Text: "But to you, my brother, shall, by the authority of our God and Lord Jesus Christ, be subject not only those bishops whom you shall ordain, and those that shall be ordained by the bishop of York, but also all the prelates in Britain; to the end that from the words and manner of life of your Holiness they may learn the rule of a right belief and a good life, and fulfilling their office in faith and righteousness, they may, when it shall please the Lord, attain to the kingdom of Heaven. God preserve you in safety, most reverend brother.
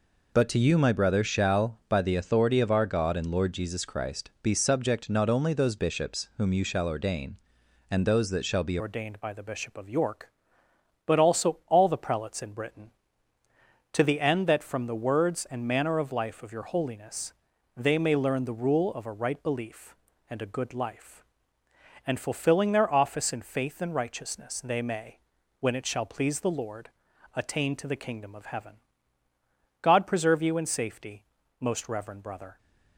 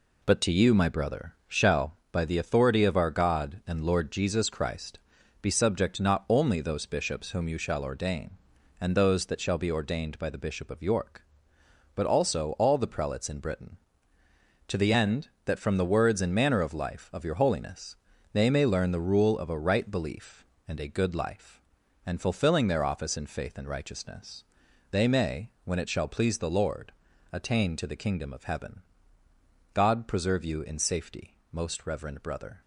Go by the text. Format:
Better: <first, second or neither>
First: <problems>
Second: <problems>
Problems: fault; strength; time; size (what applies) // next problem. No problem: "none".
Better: second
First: changes voice at "ordained"; from 8.7 s on; 23.8 s long // pauses between "Holiness" and "they"; at 17.3 s; 0.42 s long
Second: pauses between "Holiness" and "they"; slight; at 17.9 s; 0.36 s long